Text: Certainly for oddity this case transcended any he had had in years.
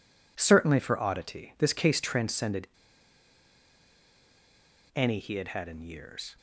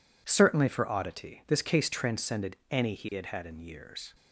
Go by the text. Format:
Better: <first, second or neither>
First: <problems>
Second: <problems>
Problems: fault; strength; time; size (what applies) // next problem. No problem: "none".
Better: second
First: pauses between "transcended" and "any"; strong; at 2.6 s; 2.2 s long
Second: none